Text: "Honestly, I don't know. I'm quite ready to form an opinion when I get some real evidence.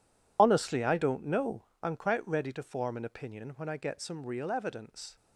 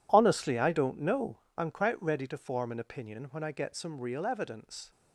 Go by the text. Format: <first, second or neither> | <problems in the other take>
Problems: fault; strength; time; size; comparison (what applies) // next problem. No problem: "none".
second | loses the start of "Honestly"; at 0.3 s; 50 ms